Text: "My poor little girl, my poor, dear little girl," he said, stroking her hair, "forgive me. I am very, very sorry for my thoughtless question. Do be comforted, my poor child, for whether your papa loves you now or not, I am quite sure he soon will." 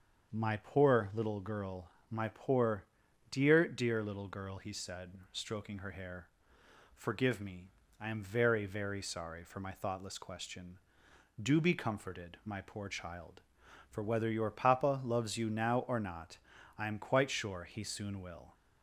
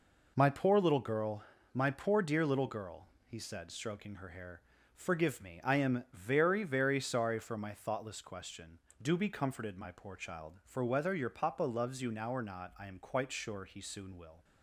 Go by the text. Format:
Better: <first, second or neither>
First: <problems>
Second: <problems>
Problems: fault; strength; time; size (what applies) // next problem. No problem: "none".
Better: second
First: starts louder than the rest; until 1.3 s; 7 dB // says "dear" twice; at 3.6 s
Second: none